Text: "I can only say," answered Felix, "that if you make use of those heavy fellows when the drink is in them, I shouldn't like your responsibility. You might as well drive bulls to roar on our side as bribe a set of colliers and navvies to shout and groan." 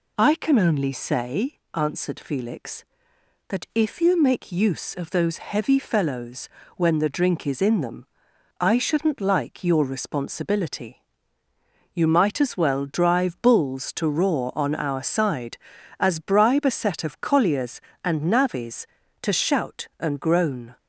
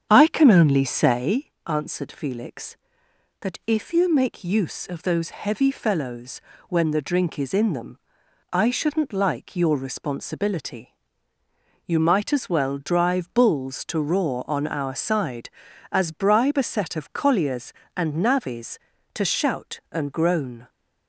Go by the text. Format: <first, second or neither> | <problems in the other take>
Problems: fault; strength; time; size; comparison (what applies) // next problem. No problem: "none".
first | starts louder than the rest; strong; until 1.5 s; 8 dB // pauses between "fellows" and "when"; slight; at 6.4 s; 0.28 s long; slight in the first